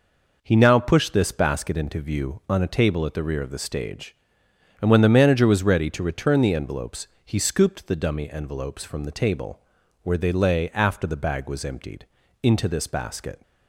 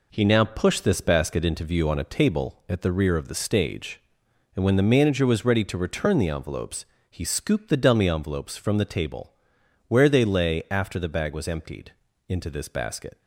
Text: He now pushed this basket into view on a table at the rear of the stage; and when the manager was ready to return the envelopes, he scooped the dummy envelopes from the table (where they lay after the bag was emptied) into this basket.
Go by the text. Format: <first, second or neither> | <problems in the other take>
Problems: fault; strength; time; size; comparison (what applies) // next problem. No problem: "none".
neither | none